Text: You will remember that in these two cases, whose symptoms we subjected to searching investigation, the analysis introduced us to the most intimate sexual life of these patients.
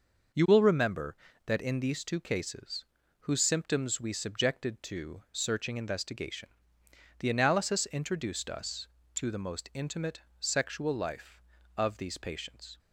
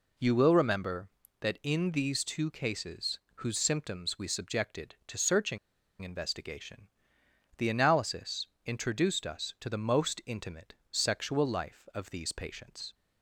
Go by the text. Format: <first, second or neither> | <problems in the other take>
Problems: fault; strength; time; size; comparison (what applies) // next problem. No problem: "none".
first | pauses between "searching" and "investigation"; at 5.5 s; 0.43 s long // pauses between "analysis" and "introduced"; slight; at 8.4 s; 0.18 s long // pauses between "intimate" and "sexual"; slight; at 10.7 s; 0.16 s long; slight in the first